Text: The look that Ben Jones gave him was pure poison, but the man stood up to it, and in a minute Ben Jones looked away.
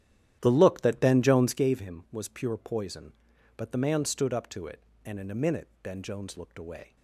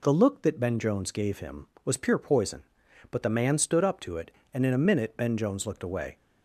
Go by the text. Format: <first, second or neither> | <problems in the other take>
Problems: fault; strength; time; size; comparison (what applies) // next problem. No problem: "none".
second | starts louder than the rest; strong; until 1.7 s; 12 dB